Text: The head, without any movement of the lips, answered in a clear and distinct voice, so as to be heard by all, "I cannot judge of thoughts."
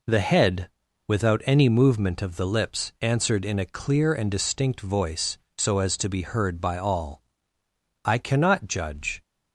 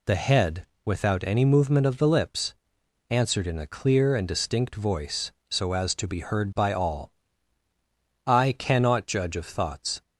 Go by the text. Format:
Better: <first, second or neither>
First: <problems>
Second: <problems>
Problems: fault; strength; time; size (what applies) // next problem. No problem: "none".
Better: second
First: stops before "of thoughts"; at 9.2 s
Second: none